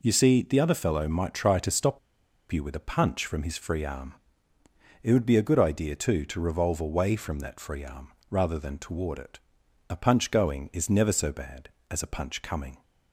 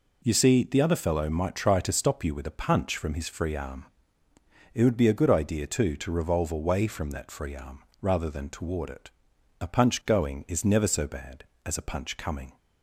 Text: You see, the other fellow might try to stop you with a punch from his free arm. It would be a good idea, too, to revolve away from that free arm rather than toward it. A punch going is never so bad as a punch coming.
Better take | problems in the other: second | pauses between "stop" and "you"; noticeable; at 1.9 s; 0.52 s long // pauses between "arm" and "rather"; slight; at 8.1 s; 0.18 s long; slight in the second

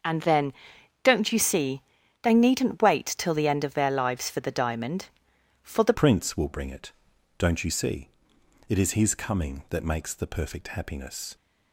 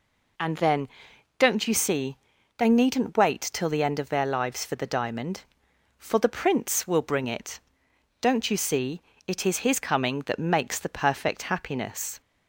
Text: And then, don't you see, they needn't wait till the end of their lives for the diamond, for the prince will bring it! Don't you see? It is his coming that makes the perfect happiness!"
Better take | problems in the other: second | starts louder than the rest; until 1.5 s; 6.5 dB // changes voice at "prince"; from 5.9 s on; 5.4 s long

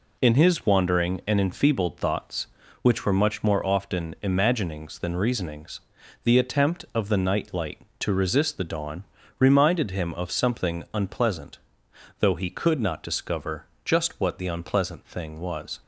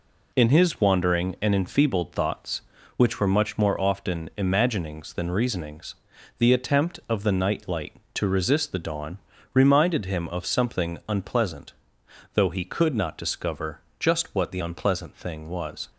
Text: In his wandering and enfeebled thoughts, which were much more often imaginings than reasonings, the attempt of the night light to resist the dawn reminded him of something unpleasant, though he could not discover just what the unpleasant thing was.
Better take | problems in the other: neither | pauses between "dawn" and "reminded"; slight; the same in both // pauses between "discover" and "just"; slight; the same in both

